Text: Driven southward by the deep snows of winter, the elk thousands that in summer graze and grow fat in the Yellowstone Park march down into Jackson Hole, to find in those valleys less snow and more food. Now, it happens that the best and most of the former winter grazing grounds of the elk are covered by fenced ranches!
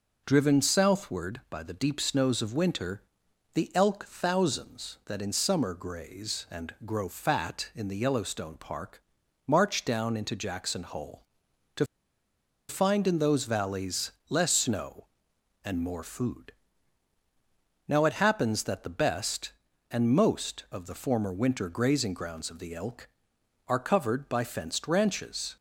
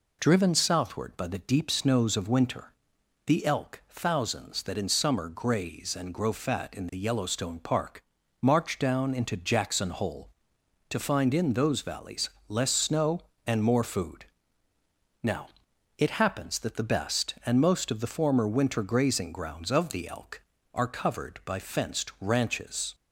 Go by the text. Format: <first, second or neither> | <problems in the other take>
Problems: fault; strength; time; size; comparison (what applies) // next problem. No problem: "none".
second | pauses between "Park" and "march"; at 9.0 s; 0.44 s long; also in the second // pauses between "to" and "find"; noticeable; at 11.8 s; 0.85 s long // pauses between "valleys" and "less"; slight; at 14.1 s; 0.18 s long; slight in the second